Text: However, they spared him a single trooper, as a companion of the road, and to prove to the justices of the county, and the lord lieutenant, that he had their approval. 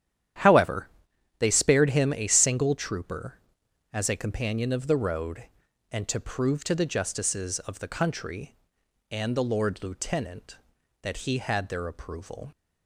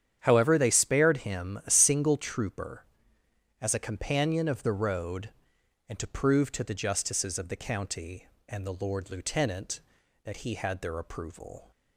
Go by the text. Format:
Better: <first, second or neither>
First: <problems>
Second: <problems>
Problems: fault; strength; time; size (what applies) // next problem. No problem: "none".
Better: second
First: starts louder than the rest; strong; until 1.9 s; 10.5 dB // says "country" for "county"; at 7.8 s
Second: starts louder than the rest; strong; until 1.2 s; 9 dB